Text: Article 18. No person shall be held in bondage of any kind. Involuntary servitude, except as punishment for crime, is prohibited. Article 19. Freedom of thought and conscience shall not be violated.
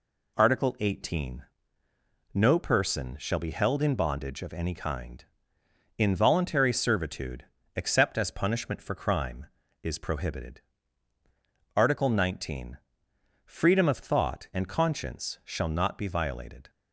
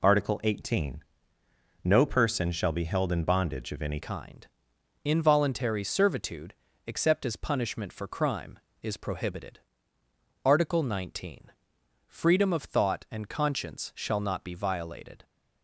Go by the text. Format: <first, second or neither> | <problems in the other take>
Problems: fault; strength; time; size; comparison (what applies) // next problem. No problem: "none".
first | changes voice at "kind"; from 4.0 s on; 11.2 s long